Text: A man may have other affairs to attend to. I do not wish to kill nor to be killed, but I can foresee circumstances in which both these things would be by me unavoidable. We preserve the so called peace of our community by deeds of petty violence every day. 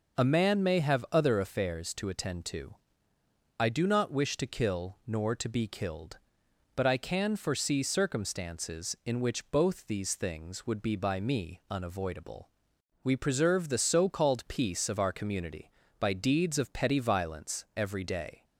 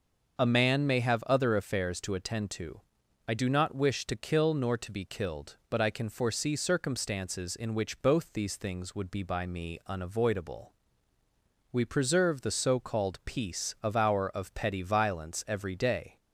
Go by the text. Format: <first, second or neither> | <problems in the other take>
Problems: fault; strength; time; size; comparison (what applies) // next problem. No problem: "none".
first | starts louder than the rest; until 1.4 s; 6 dB // skips "community by deeds"; at 14.3 s